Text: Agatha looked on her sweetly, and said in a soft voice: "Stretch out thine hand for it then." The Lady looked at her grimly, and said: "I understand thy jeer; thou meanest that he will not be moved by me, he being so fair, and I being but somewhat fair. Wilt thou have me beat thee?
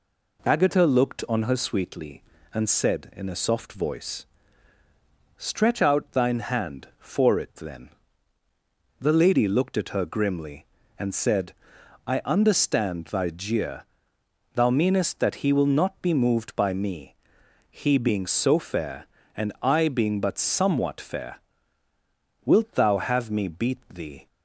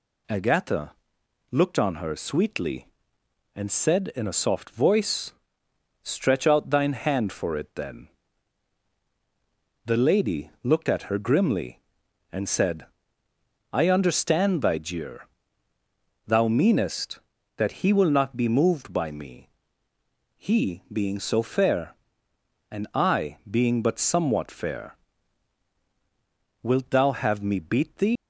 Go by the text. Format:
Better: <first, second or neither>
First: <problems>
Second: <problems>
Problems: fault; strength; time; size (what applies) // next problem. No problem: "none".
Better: first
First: none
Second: pauses between "Agatha" and "looked"; noticeable; at 0.9 s; 0.58 s long // leaves "thee" unfinished; at 28.1 s; 100 ms